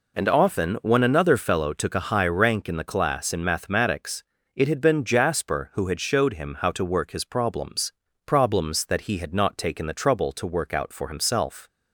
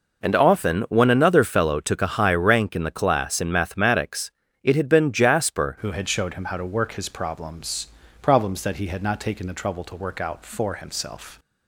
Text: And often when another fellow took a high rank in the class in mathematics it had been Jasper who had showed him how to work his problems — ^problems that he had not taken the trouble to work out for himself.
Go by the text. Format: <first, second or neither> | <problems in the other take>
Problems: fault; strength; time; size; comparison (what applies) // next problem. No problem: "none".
first | pauses between "mathematics" and "it"; slight; at 4.3 s; 0.32 s long; slight in the first // changes voice at "who"; from 5.8 s on; 5.5 s long